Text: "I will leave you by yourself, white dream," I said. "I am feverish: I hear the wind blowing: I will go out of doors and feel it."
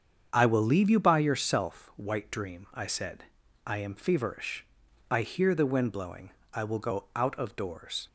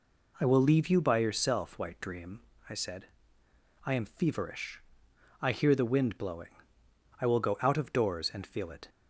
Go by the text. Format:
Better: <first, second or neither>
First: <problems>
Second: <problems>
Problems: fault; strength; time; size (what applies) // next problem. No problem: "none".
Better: second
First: starts louder than the rest; strong; until 1.3 s; 7.5 dB // stops before "and feel it"; at 8.0 s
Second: none